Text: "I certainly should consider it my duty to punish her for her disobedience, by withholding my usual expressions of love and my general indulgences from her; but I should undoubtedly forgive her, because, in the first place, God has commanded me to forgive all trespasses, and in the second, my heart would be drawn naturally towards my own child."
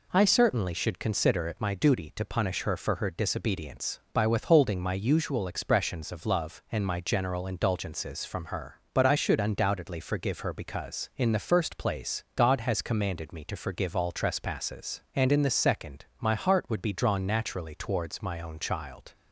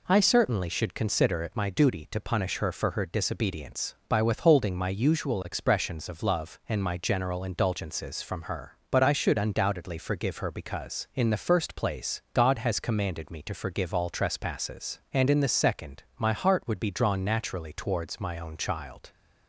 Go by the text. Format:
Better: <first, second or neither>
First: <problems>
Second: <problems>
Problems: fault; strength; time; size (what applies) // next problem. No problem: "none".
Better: neither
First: none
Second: none